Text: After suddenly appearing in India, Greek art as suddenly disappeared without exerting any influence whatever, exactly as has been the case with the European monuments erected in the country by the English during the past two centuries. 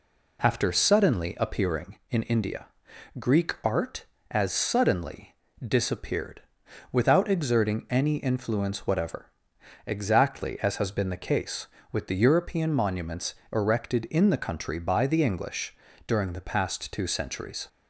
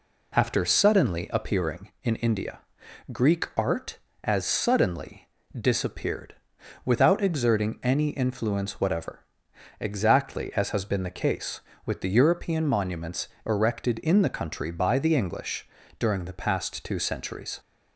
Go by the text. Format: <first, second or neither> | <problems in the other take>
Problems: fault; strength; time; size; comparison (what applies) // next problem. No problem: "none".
neither | pauses between "suddenly" and "disappeared"; slight; the same in both // pauses between "disappeared" and "without"; noticeable; the same in both // pauses between "monuments" and "erected"; slight; the same in both // pauses between "English" and "during"; slight; the same in both